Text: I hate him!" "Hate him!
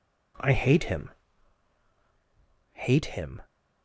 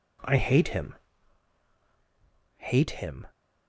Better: neither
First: none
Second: none

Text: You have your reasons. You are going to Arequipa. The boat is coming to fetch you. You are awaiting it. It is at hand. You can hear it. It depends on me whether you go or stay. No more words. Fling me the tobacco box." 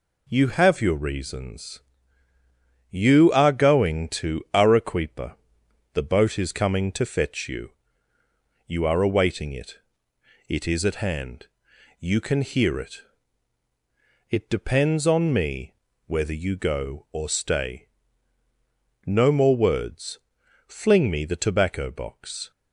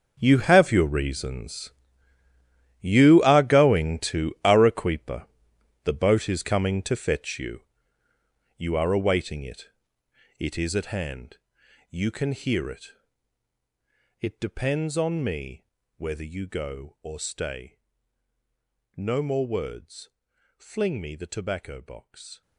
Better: first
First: pauses between "me" and "whether"; slight; at 15.7 s; 0.32 s long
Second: gets quieter; strong; throughout; 17 dB // pauses between "me" and "whether"; slight; at 15.6 s; 0.32 s long

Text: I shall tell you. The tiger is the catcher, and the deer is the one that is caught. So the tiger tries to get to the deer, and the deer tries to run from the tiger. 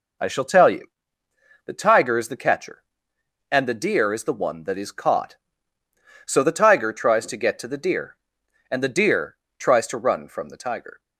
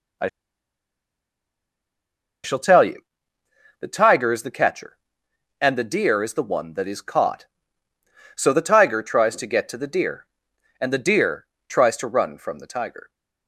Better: first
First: pauses between "deer" and "tries"; slight; at 9.3 s; 0.24 s long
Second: pauses between "I" and "shall"; strong; at 0.2 s; 2.1 s long // pauses between "deer" and "tries"; slight; at 11.4 s; 0.24 s long

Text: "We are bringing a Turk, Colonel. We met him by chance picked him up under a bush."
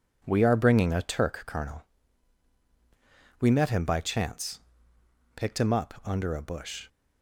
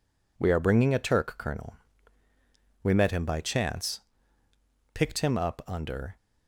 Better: first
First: pauses between "chance" and "picked"; noticeable; at 4.6 s; 0.74 s long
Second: pauses between "chance" and "picked"; noticeable; at 3.9 s; 0.92 s long // stops before "a bush"; at 6.1 s

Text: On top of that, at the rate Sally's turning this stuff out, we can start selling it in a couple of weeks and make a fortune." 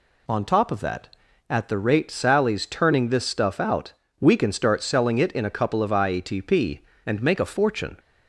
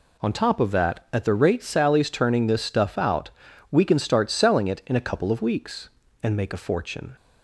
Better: second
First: says "ietp" for "weeks"; at 5.8 s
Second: none

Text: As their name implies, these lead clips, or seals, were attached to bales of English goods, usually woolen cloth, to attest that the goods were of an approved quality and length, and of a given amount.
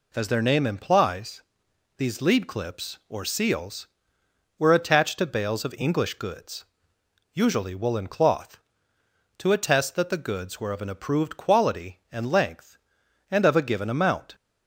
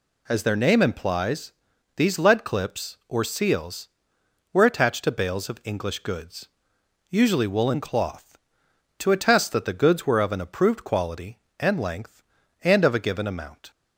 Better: neither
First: none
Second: none

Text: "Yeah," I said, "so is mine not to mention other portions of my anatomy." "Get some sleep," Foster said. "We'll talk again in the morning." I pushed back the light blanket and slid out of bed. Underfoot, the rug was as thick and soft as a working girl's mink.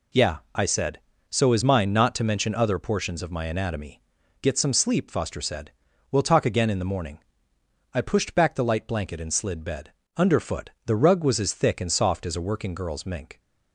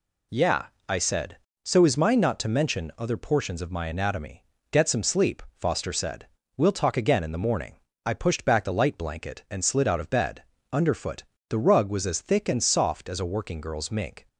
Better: second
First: skips "out of"; at 9.6 s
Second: none

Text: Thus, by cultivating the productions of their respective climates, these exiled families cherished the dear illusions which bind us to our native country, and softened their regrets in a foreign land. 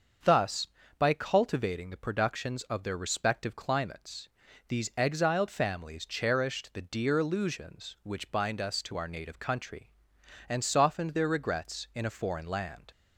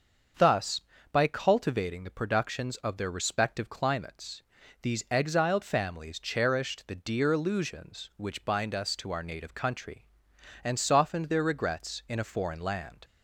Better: neither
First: starts louder than the rest; until 1.5 s; 6.5 dB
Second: starts louder than the rest; until 1.6 s; 6.5 dB

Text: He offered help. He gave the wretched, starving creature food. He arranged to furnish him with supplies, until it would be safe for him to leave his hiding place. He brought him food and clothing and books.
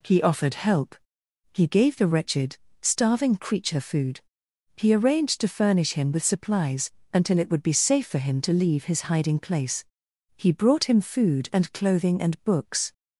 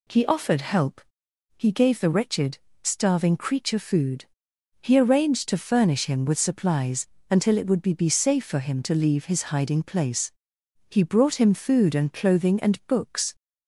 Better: first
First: none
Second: says "be" twice; at 7.9 s

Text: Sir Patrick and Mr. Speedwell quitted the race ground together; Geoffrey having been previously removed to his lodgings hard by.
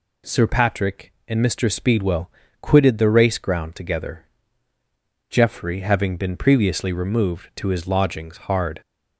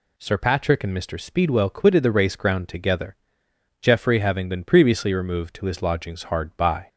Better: second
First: pauses between "Speedwell" and "quitted"; slight; at 2.3 s; 0.32 s long // stops before "by"; at 8.8 s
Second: none

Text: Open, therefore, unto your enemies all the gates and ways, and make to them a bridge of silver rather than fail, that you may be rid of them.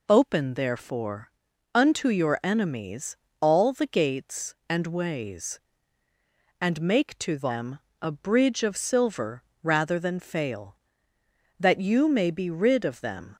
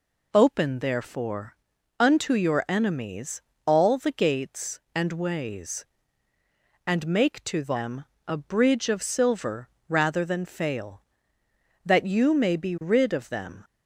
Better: neither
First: pauses between "enemies" and "all"; slight; at 3.1 s; 0.24 s long // pauses between "them" and "a"; slight; at 7.7 s; 0.24 s long // pauses between "silver" and "rather"; slight; at 9.4 s; 0.18 s long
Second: pauses between "enemies" and "all"; slight; at 3.4 s; 0.24 s long // pauses between "them" and "a"; slight; at 8.0 s; 0.24 s long // pauses between "silver" and "rather"; slight; at 9.6 s; 0.18 s long

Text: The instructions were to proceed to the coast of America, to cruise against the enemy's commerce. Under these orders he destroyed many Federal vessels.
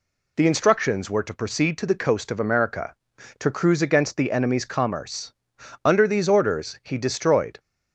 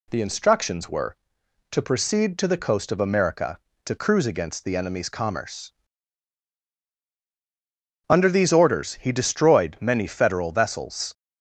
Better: second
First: stops before "many Federal vessels"; at 7.5 s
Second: none

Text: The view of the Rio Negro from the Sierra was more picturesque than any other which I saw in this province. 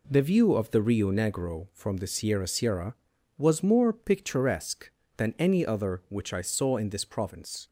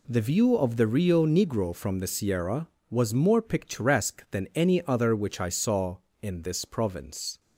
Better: second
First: says "Sierra" twice; at 2.4 s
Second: none

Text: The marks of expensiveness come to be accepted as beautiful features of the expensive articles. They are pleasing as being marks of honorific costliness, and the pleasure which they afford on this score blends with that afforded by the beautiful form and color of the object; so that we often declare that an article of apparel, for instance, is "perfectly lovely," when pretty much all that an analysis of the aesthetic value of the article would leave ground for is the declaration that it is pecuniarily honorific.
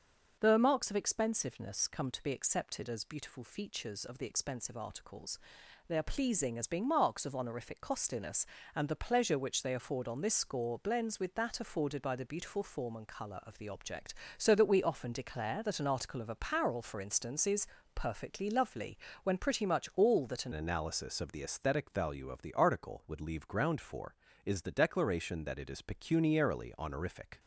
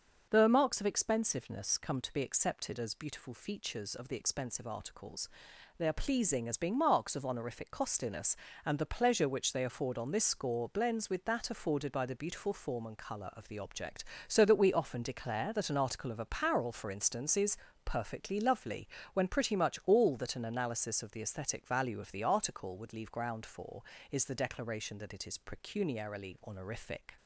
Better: second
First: starts louder than the rest; until 1.4 s; 6.5 dB // pauses between "is" and "perfectly"; slight; at 17.6 s; 0.28 s long // changes voice at "analysis"; from 20.5 s on; 6.8 s long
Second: starts louder than the rest; until 1.3 s; 6.5 dB // pauses between "is" and "perfectly"; slight; at 17.5 s; 0.28 s long

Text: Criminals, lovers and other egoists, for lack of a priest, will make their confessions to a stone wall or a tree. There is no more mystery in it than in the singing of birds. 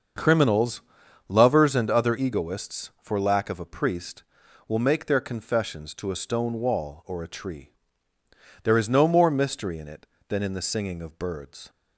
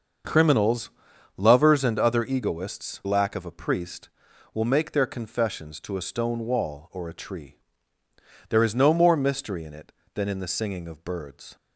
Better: first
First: starts louder than the rest; until 1.6 s; 6.5 dB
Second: starts louder than the rest; until 1.7 s; 6.5 dB // skips "for"; at 3.0 s

